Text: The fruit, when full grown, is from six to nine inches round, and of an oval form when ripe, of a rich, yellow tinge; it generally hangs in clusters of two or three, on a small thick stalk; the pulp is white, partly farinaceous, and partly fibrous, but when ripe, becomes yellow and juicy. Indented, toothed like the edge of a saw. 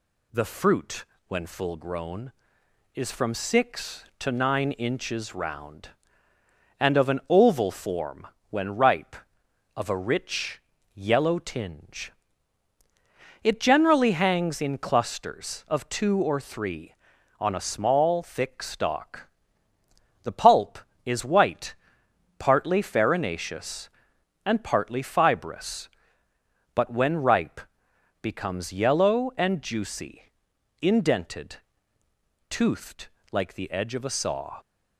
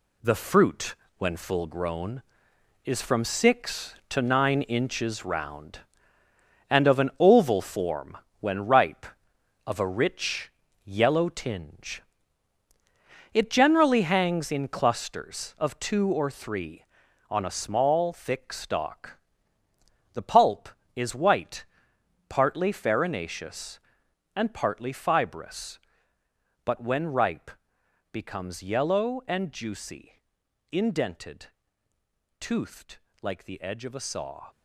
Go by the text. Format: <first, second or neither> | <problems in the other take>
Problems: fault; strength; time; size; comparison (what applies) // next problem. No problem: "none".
first | gets quieter; strong; throughout; 7.5 dB // pauses between "form" and "when"; slight; at 8.1 s; 0.22 s long; slight in the first // pauses between "toothed" and "like"; slight; at 32.9 s; 0.24 s long; slight in the first